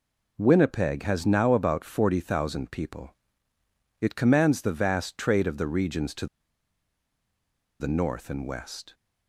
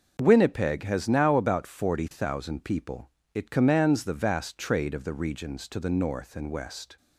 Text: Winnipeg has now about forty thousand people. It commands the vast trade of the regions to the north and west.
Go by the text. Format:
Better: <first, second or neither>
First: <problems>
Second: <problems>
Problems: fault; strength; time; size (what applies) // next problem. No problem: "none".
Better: second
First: pauses between "to" and "the"; strong; at 6.2 s; 1.5 s long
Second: none